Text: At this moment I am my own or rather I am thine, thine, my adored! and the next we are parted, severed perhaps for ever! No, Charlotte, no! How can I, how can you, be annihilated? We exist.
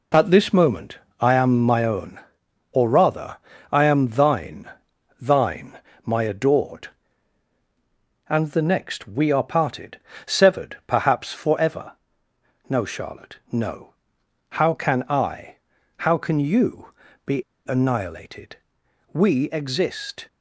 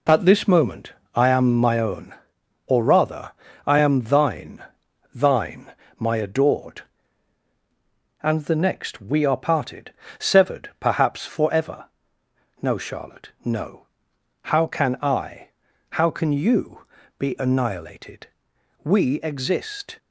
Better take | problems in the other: second | pauses between "moment" and "I"; slight; at 0.9 s; 0.20 s long; slight in the second // pauses between "rather" and "I"; slight; at 3.3 s; 0.34 s long; slight in the second // pauses between "be" and "annihilated"; slight; at 17.4 s; 0.28 s long

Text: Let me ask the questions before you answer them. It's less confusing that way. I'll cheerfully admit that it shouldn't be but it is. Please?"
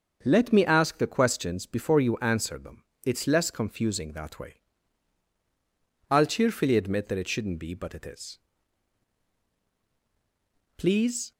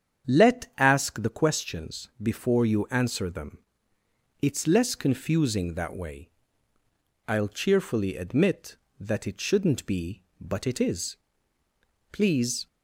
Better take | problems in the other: first | starts louder than the rest; strong; until 1.3 s; 8 dB; also in the first // skips "me"; at 0.7 s

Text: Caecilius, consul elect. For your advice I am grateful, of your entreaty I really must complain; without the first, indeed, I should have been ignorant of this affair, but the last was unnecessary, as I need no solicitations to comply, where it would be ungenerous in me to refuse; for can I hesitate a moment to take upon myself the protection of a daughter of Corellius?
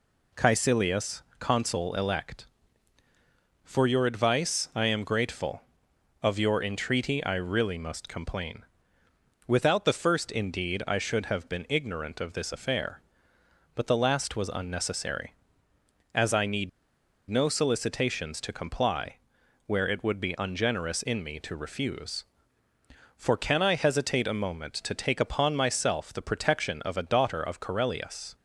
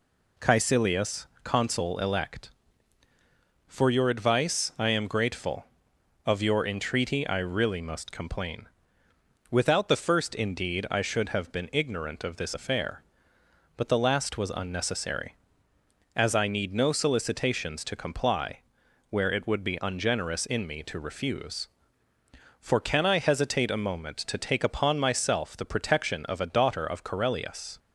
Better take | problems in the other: second | pauses between "need" and "no"; noticeable; at 16.6 s; 0.60 s long

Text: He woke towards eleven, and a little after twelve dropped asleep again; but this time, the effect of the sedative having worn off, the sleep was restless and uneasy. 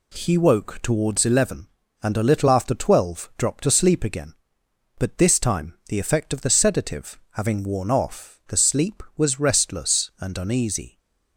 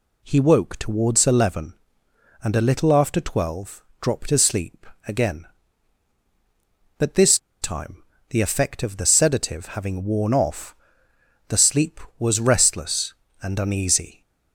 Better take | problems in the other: first | pauses between "twelve" and "dropped"; slight; at 3.8 s; 0.16 s long // pauses between "asleep" and "again"; slight; at 4.8 s; 0.20 s long // pauses between "this" and "time"; slight; at 7.3 s; 0.23 s long

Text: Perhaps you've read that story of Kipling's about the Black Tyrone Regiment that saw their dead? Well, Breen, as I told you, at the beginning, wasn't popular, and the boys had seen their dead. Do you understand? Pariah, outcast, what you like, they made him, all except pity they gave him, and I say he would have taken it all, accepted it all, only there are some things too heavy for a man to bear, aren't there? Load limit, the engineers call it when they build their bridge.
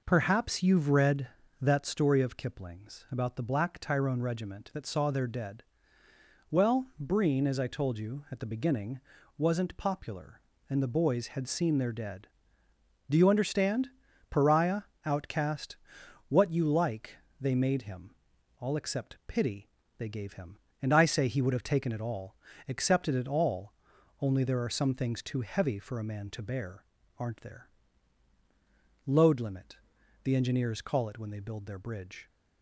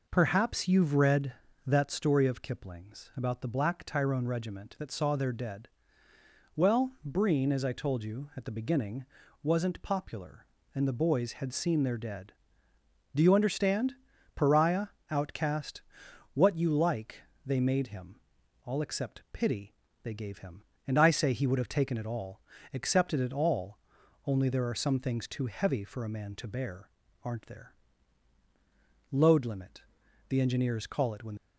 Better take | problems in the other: first | pauses between "pity" and "they"; slight; at 19.7 s; 0.30 s long; slight in the first // stops before "they build their bridge"; at 31.3 s

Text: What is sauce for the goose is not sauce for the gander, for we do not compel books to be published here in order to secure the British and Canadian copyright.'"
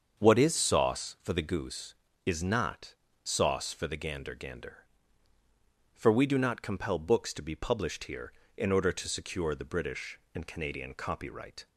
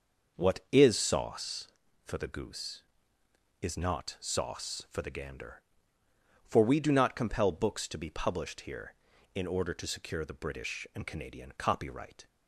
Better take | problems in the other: second | starts louder than the rest; until 1.2 s; 6.5 dB; noticeable in the second // pauses between "not" and "sauce"; slight; at 2.9 s; 0.28 s long // says "gander" twice; at 4.3 s

